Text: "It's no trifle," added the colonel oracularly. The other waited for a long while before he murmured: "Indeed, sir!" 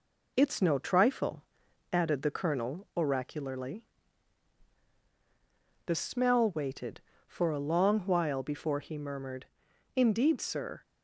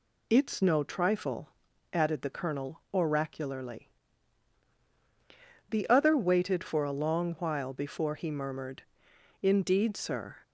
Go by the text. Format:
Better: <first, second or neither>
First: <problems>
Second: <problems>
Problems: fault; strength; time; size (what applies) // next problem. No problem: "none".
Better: second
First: says "smell" for "other"; at 5.9 s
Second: none